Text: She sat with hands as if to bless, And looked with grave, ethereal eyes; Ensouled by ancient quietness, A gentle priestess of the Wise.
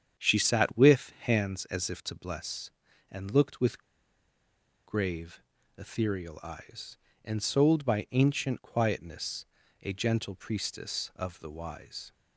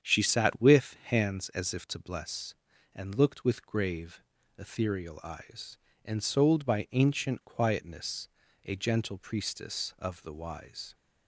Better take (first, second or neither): second